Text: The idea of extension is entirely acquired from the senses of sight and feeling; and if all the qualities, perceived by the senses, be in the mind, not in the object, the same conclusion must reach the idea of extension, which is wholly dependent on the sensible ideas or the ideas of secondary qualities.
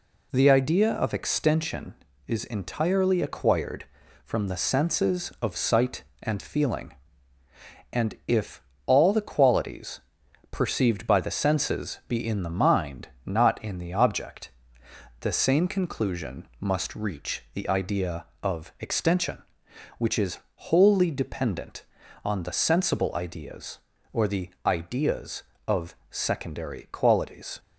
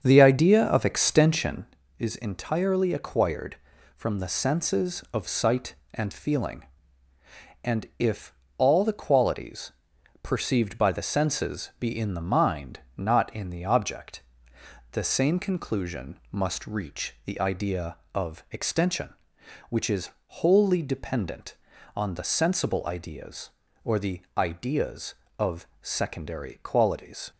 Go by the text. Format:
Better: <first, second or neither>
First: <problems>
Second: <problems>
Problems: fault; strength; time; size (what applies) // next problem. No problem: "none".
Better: first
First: pauses between "if" and "all"; slight; at 8.6 s; 0.24 s long // pauses between "is" and "wholly"; slight; at 20.3 s; 0.32 s long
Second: starts louder than the rest; until 1.7 s; 7 dB // pauses between "if" and "all"; slight; at 8.3 s; 0.24 s long // pauses between "is" and "wholly"; slight; at 20.0 s; 0.32 s long